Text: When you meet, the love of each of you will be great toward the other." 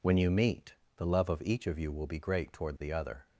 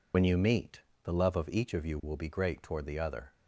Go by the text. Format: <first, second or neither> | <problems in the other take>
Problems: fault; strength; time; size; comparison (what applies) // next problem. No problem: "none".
first | loses the start of "When"; at 0.1 s; 55 ms